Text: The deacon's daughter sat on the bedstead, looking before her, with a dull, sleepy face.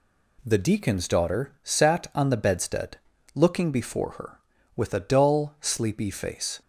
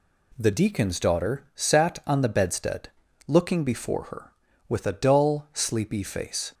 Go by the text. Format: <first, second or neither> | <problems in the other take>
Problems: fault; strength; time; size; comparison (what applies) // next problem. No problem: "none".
neither | none